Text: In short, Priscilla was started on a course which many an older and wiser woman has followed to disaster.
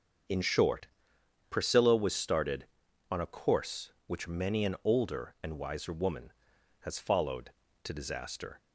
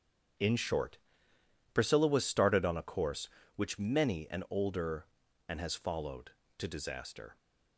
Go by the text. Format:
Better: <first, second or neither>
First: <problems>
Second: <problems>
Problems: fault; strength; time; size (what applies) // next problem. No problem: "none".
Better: first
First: starts louder than the rest; until 1.9 s; 7 dB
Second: starts louder than the rest; strong; until 2.1 s; 8 dB // skips "wiser woman"; at 5.6 s